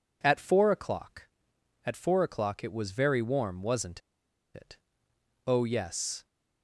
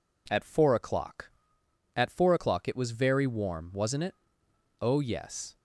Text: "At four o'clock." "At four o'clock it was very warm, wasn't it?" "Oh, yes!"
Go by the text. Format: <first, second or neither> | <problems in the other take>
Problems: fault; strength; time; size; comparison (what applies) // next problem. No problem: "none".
second | pauses between "wasn't" and "it"; noticeable; at 3.9 s; 0.54 s long